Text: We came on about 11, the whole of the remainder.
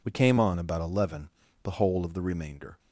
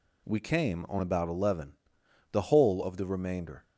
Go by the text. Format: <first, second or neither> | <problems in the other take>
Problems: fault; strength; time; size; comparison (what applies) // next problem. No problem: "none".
neither | none